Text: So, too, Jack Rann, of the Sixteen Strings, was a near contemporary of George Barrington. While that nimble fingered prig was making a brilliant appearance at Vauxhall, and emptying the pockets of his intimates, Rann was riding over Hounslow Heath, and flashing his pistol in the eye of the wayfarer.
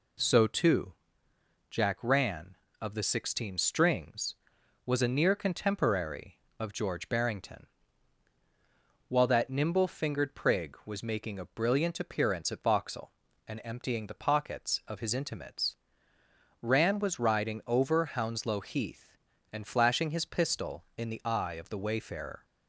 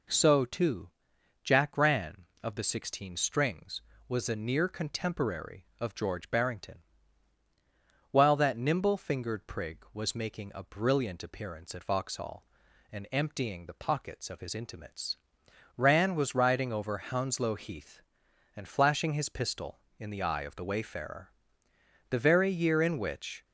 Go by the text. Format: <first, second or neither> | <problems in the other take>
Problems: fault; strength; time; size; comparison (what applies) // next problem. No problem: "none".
first | goes on to say "The very year in which"; from 22.0 s on; 1.3 s long